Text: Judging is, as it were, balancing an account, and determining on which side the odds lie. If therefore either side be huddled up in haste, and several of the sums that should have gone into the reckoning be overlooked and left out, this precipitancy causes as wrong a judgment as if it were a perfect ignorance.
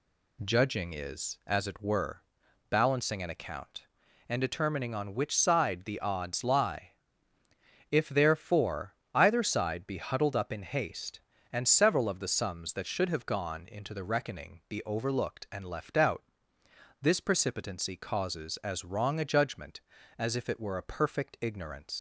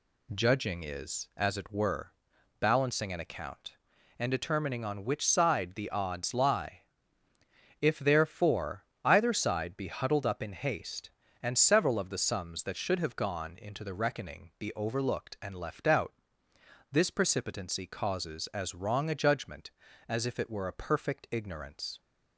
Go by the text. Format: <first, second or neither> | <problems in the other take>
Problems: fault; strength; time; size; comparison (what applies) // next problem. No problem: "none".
second | pauses between "therefore" and "either"; slight; at 8.9 s; 0.20 s long; slight in the second // leaves "ignorance" unfinished; at 21.9 s; 100 ms